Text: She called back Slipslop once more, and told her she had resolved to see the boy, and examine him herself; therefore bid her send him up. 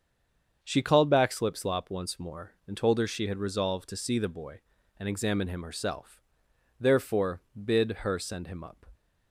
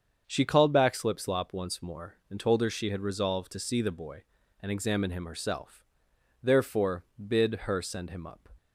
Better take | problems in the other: second | stays silent before the first word; slight; until 0.6 s; 0.6 s long // starts louder than the rest; until 1.6 s; 7 dB; also in the second // pauses between "therefore" and "bid"; slight; at 7.4 s; 0.24 s long; slight in the second

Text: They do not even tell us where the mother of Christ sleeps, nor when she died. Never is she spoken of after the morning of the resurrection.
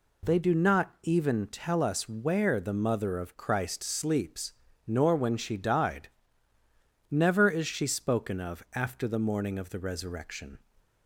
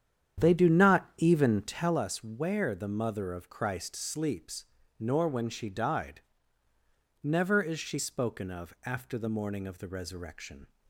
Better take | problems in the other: first | starts louder than the rest; strong; until 2.1 s; 9 dB

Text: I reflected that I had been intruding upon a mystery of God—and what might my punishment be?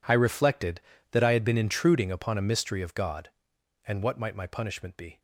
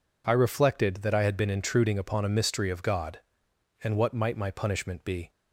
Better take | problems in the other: second | gets quieter; strong; throughout; 17 dB

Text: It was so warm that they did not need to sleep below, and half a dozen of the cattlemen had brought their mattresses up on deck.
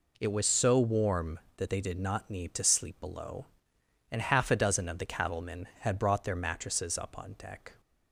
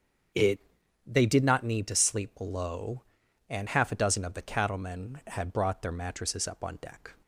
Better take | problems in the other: first | starts louder than the rest; strong; until 1.7 s; 7 dB // skips "was so warm that"; at 0.8 s

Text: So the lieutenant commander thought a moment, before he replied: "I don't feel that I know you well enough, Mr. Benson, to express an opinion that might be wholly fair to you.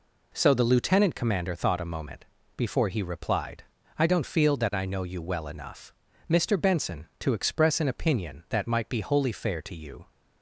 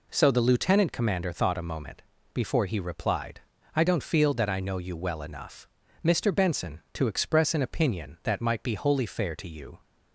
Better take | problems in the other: neither | none

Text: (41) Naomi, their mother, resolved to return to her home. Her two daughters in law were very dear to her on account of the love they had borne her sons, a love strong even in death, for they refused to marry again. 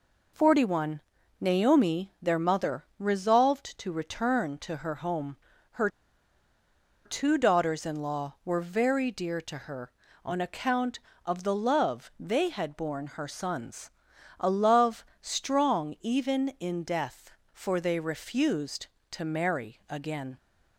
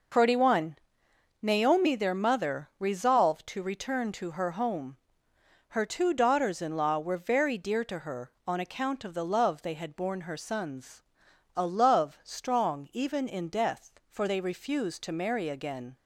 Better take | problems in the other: second | pauses between "Her" and "two"; at 5.8 s; 1.1 s long // pauses between "love" and "strong"; slight; at 15.0 s; 0.20 s long

